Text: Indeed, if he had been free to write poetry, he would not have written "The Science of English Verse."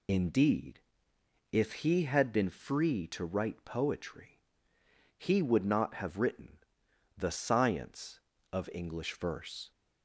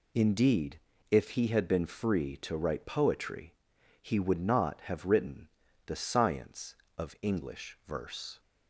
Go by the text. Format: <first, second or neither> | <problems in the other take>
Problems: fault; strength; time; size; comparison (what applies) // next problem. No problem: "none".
second | loses the start of "Indeed"; at 0.0 s; 40 ms // pauses between "written" and "The"; noticeable; at 6.5 s; 0.58 s long; slight in the second